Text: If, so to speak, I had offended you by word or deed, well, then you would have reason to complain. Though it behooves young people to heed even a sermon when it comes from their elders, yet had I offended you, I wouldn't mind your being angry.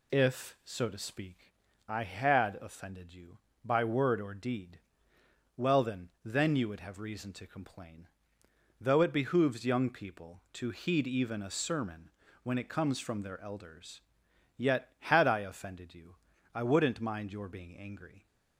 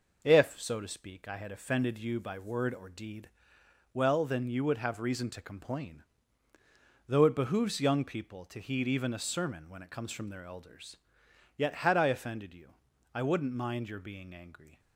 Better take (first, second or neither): second